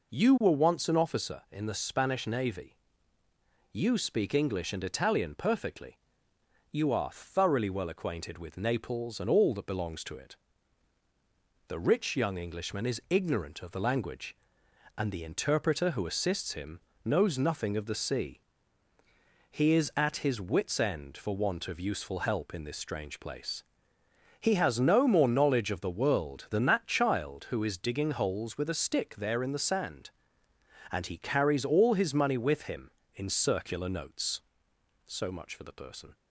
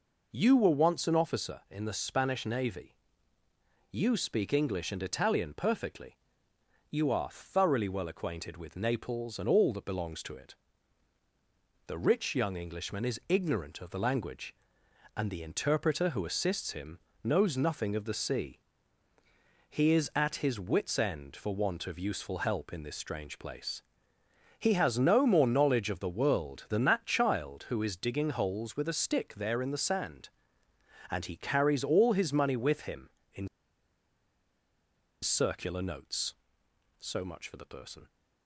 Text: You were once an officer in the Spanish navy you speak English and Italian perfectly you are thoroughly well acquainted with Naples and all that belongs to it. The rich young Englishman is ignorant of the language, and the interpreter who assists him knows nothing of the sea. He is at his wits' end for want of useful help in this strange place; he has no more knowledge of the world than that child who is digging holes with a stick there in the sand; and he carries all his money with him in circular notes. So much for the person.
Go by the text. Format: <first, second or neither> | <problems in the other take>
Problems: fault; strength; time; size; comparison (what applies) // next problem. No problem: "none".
first | pauses between "navy" and "you"; noticeable; at 2.9 s; 0.98 s long; noticeable in the first // pauses between "perfectly" and "you"; noticeable; at 6.1 s; 0.74 s long; noticeable in the first // pauses between "him" and "knows"; slight; at 16.9 s; 0.24 s long; slight in the first // pauses between "in" and "circular"; strong; at 33.4 s; 1.7 s long